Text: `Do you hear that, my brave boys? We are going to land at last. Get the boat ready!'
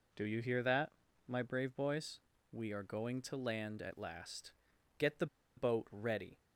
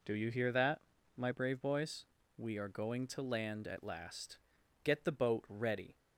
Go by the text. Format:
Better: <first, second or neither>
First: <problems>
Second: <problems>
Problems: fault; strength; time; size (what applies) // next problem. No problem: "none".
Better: second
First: pauses between "the" and "boat"; slight; at 5.2 s; 0.31 s long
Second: none